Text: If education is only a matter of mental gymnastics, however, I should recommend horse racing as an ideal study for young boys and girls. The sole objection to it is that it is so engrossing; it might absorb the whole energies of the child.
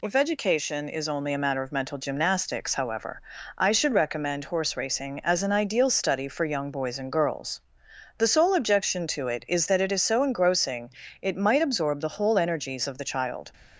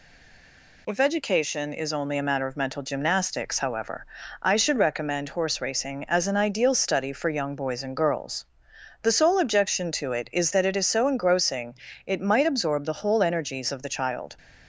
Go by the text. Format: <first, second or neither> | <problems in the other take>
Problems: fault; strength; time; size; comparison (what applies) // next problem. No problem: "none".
first | stays silent before the first word; slight; until 0.8 s; 0.8 s long